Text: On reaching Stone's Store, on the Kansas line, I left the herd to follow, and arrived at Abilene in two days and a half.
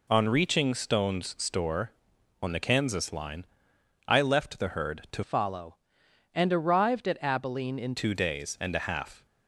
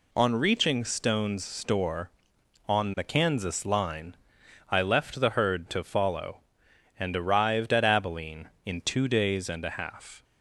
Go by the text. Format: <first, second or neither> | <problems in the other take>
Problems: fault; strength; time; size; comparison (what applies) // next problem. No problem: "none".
second | changes voice from "follow" to "in"; from 5.2 to 7.9 s; 2.7 s long